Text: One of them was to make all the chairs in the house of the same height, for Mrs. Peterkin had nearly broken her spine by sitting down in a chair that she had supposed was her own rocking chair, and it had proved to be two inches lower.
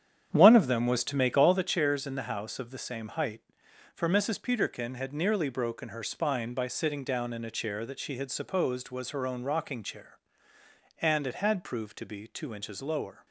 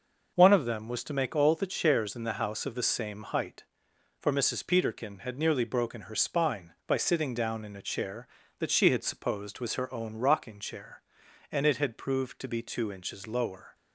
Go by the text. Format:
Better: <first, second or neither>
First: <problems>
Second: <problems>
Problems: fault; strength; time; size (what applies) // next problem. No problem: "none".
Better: second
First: starts louder than the rest; strong; until 1.6 s; 9 dB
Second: none